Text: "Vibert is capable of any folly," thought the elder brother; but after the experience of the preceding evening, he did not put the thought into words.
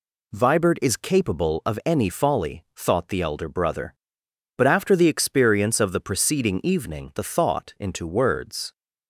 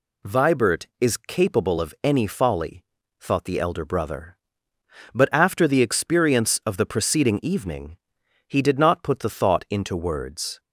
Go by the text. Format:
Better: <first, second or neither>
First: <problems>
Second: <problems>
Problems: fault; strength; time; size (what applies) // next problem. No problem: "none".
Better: second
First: skips "he did not put"; at 7.1 s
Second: none